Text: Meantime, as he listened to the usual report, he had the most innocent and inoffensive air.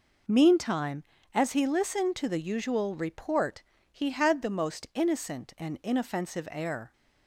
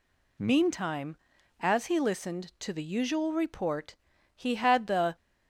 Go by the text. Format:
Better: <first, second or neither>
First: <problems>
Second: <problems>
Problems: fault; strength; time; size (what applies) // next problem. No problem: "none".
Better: first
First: none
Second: stops before "most innocent and inoffensive air"; at 5.1 s